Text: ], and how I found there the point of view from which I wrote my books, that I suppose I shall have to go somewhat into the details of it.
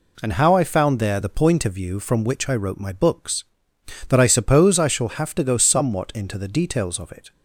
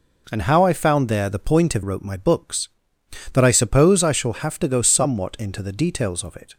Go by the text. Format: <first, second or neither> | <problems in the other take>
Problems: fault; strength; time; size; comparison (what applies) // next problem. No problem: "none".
first | skips "view from which I"; at 1.8 s